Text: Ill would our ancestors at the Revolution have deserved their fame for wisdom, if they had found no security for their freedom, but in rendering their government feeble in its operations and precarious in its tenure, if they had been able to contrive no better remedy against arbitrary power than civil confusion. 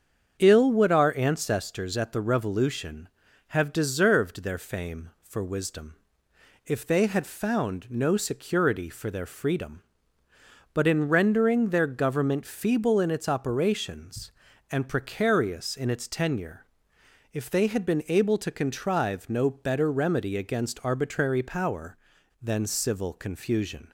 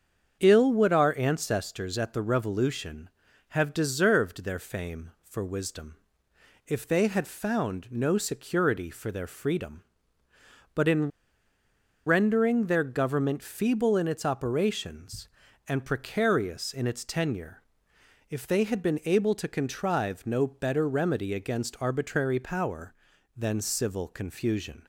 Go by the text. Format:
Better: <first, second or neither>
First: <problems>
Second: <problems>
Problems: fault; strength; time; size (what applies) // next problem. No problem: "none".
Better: first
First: starts louder than the rest; strong; until 1.4 s; 7.5 dB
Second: starts louder than the rest; strong; until 1.4 s; 7.5 dB // pauses between "in" and "rendering"; noticeable; at 11.0 s; 0.97 s long